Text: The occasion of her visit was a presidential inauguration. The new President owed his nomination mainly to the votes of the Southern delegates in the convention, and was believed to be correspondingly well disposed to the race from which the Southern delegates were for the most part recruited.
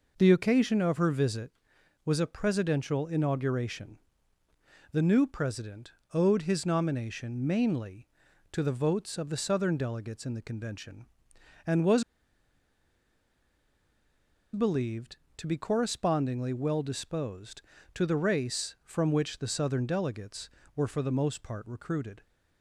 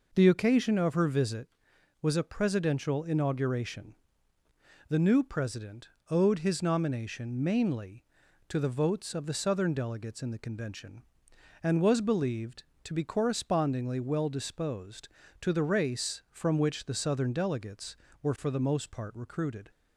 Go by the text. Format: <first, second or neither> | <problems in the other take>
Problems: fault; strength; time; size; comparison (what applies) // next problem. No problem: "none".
second | pauses between "President" and "owed"; slight; at 5.8 s; 0.24 s long; slight in the second // pauses between "was" and "believed"; strong; at 12.0 s; 2.5 s long